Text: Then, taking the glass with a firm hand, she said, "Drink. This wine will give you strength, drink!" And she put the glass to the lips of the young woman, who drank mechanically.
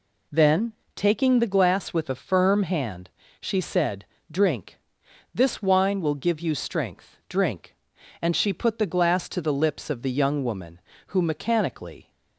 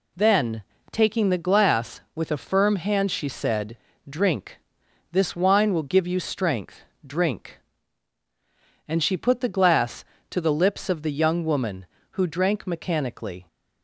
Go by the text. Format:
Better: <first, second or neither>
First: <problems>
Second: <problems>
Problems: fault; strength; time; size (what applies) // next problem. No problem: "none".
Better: second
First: skips "drank"; at 11.2 s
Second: none